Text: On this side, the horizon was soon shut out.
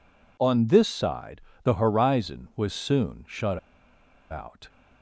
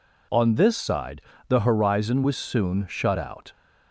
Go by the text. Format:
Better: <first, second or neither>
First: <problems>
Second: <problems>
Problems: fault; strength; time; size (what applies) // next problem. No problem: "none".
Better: second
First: pauses between "shut" and "out"; noticeable; at 3.5 s; 0.73 s long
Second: none